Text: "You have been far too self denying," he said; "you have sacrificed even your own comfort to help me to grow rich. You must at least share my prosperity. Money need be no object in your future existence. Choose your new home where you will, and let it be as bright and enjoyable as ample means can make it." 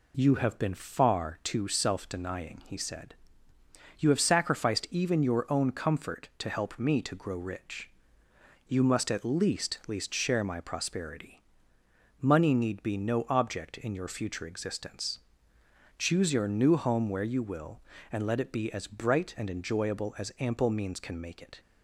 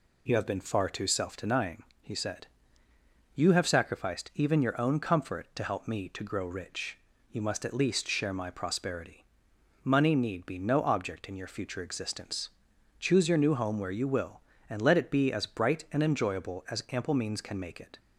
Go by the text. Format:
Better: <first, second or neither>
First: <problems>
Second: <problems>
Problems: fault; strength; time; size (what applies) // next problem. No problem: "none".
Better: second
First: says "least" twice; at 9.8 s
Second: none